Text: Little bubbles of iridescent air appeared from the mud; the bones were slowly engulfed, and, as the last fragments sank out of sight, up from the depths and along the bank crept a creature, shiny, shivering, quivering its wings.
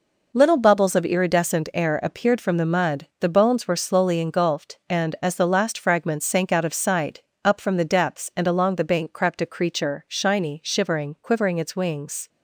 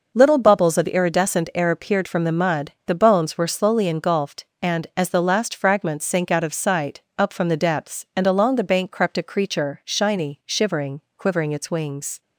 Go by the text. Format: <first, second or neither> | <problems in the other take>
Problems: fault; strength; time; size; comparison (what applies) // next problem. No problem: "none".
neither | none